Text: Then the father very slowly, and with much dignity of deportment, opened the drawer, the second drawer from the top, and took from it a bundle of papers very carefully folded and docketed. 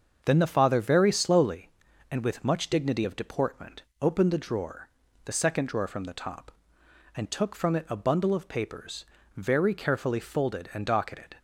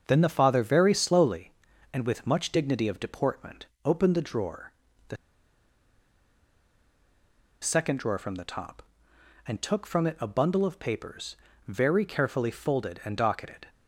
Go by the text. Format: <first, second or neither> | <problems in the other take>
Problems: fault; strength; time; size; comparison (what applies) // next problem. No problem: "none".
first | starts louder than the rest; until 1.0 s; 6.5 dB; also in the first // pauses between "the" and "second"; strong; at 5.1 s; 2.4 s long // pauses between "papers" and "very"; slight; at 11.3 s; 0.30 s long; slight in the first